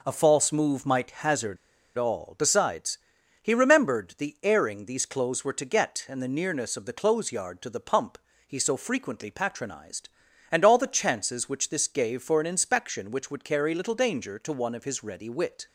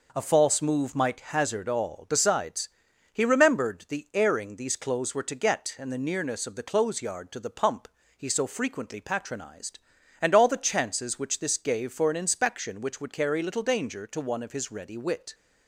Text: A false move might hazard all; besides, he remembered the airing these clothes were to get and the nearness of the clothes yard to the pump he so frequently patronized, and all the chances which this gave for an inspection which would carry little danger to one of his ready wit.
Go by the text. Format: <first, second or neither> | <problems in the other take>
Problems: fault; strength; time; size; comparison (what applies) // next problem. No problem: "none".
second | pauses between "hazard" and "all"; at 1.5 s; 0.41 s long // pauses between "pump" and "he"; slight; at 8.1 s; 0.32 s long; slight in the second